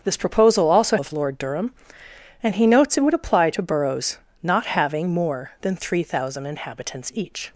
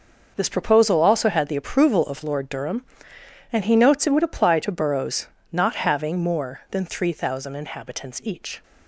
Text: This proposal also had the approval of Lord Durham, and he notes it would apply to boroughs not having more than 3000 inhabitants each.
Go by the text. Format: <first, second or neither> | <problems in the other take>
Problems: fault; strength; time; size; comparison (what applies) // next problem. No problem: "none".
second | starts louder than the rest; until 1.0 s; 7 dB // skips "had the approval"; at 0.9 s // pauses between "boroughs" and "not"; slight; at 4.1 s; 0.28 s long; slight in the second